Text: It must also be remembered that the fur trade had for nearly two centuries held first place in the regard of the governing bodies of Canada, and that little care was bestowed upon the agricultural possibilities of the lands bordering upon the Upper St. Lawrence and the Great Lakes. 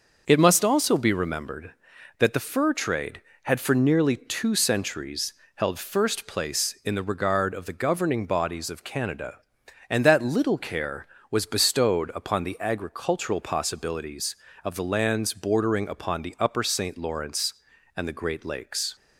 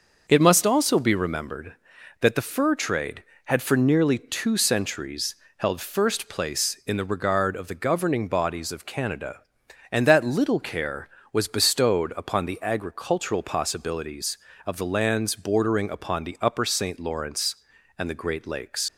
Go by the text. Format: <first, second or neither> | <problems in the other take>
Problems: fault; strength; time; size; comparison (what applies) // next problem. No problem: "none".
first | starts louder than the rest; until 1.2 s; 6 dB; noticeable in the first // pauses between "centuries" and "held"; slight; at 5.3 s; 0.22 s long; slight in the first // leaves "Lakes" unfinished; at 18.8 s; 85 ms